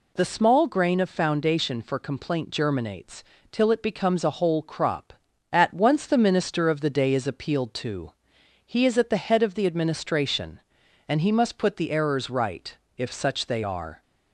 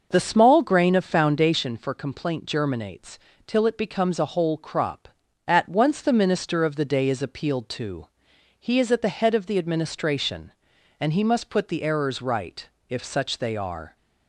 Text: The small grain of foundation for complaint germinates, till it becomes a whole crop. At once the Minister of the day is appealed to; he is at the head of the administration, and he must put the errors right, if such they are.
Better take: first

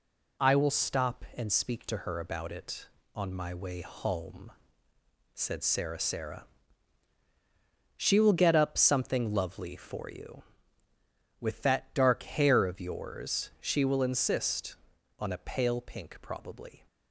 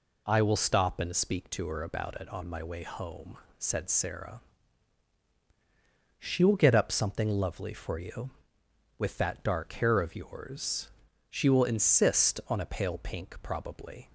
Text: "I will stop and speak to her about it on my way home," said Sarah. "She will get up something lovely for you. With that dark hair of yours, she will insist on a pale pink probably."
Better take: second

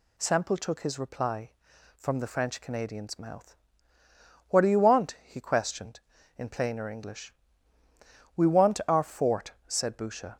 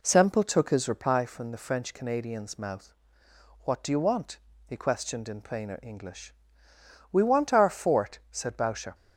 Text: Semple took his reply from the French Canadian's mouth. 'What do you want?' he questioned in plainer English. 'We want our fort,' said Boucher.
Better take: first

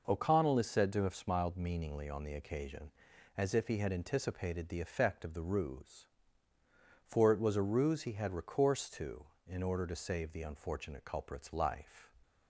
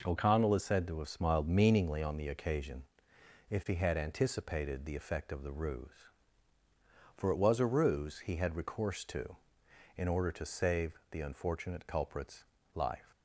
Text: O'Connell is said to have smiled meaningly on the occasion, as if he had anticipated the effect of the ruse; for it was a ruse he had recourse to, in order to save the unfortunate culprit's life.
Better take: first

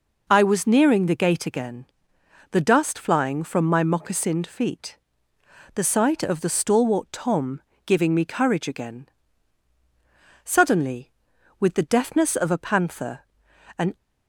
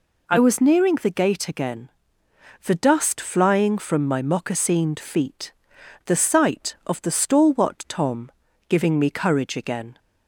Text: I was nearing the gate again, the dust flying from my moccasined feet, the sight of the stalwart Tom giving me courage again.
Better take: second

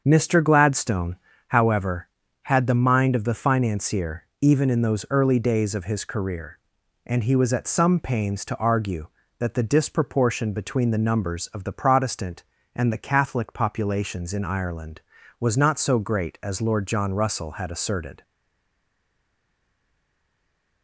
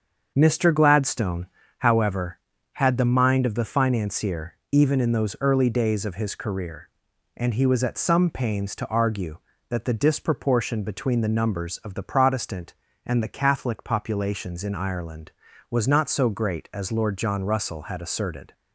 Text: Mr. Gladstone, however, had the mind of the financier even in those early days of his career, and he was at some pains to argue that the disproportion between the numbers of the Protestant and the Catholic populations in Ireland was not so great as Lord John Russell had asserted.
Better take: second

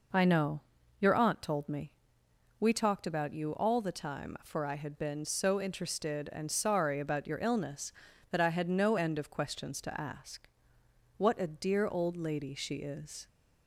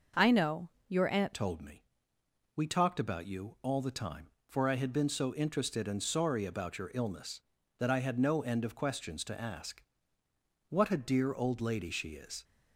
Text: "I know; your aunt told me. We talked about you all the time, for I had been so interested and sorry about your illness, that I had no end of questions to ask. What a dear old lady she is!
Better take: first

